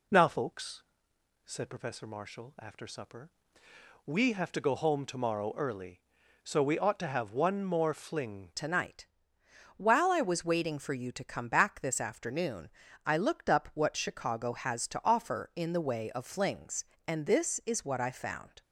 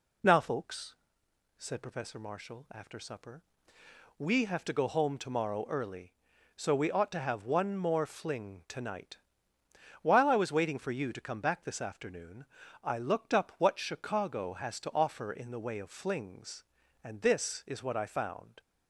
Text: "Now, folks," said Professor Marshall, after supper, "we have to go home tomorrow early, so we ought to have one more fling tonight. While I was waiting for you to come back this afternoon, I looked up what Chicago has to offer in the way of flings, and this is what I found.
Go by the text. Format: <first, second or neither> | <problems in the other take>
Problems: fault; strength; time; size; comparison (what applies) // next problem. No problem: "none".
second | changes voice at "tonight"; from 8.5 s on; 10.1 s long